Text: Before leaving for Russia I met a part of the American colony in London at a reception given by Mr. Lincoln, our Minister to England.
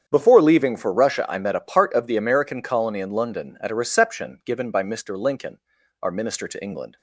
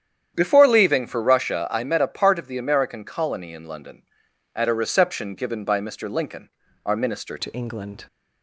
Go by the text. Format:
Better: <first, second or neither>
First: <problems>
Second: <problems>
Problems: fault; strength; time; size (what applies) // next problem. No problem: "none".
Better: first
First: starts louder than the rest; strong; until 1.1 s; 8 dB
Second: starts louder than the rest; strong; until 1.3 s; 9.5 dB // changes voice at "to"; from 7.3 s on; 0.7 s long